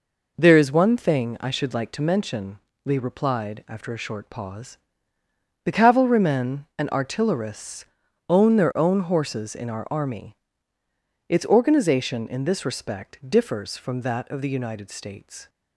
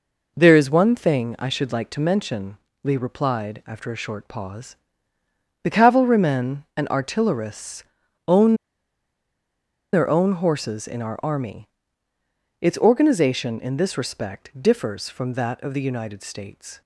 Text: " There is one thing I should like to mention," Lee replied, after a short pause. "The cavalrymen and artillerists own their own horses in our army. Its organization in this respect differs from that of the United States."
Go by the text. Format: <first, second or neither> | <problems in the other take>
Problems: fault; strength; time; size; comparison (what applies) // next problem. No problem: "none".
first | pauses between "artillerists" and "own"; at 7.8 s; 0.42 s long; also in the first // pauses between "own" and "their"; strong; at 8.5 s; 1.3 s long